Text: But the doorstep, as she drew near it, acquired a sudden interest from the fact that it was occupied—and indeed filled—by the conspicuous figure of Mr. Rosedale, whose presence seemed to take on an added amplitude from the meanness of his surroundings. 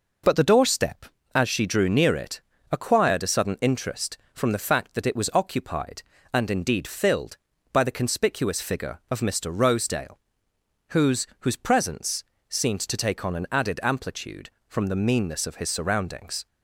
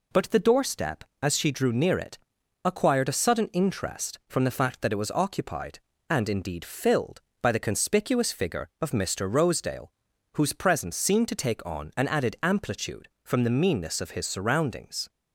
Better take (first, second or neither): second